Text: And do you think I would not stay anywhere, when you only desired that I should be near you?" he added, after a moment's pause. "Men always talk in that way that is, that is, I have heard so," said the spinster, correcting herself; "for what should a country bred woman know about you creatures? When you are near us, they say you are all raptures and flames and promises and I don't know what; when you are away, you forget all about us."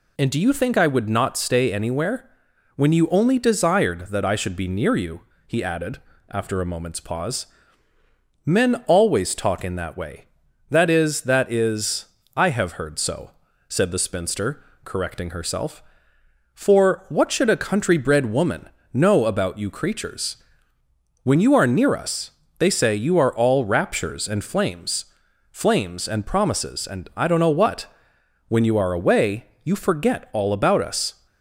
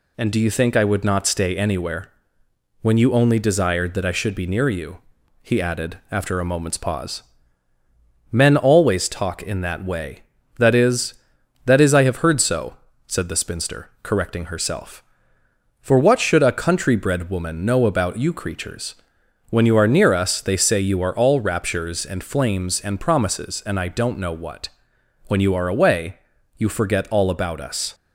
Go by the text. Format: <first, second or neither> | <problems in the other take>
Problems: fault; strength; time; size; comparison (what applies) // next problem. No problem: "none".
second | pauses between "woman" and "know"; slight; at 18.6 s; 0.24 s long // says "flames" twice; at 25.5 s